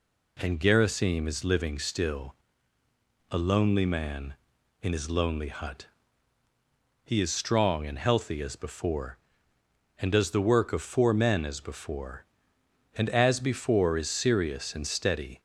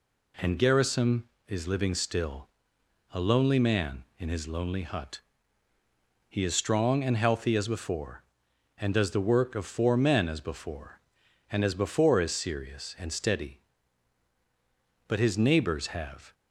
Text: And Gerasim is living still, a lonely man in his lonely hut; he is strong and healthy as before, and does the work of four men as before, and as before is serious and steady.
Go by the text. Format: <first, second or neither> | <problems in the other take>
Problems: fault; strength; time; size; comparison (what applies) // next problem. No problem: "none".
first | goes on to say "But his neighbors have"; noticeable; from 15.0 s on; 1.2 s long